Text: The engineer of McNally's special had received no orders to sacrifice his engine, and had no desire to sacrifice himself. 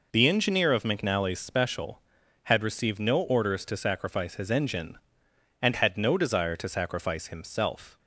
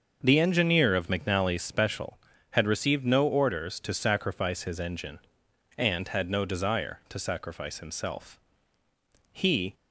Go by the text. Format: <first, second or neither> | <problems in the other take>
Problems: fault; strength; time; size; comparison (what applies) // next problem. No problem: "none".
first | starts louder than the rest; until 1.2 s; 6.5 dB // goes on to say "He"; slight; from 9.3 s on; 0.42 s long